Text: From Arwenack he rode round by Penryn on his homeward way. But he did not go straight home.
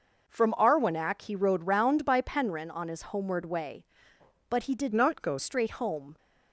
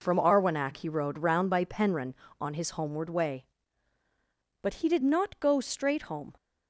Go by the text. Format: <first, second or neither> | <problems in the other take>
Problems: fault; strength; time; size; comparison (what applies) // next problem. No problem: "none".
second | changes voice from "not" to "go"; from 4.9 to 5.3 s; 0.4 s long